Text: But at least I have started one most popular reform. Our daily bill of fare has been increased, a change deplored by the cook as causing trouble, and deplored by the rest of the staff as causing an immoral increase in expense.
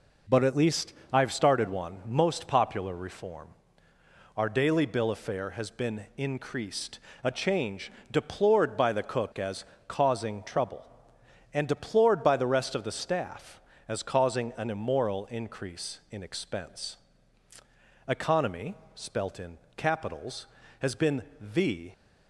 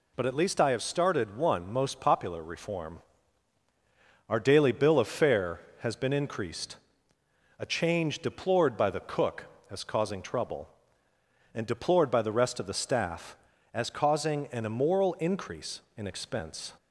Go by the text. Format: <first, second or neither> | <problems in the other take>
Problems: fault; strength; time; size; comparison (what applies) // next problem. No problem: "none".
second | pauses between "least" and "I"; slight; at 0.9 s; 0.20 s long // pauses between "change" and "deplored"; slight; at 7.8 s; 0.22 s long // pauses between "as" and "causing"; slight; at 9.6 s; 0.24 s long // goes on to say "ECONOMY spelt in capitals has been the"; strong; from 18.0 s on; 3.8 s long